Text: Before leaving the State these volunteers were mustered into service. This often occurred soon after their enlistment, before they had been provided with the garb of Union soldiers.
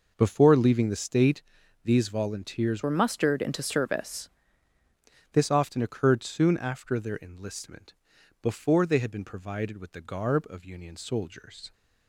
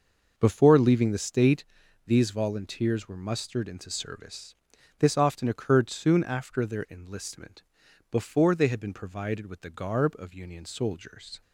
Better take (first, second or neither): second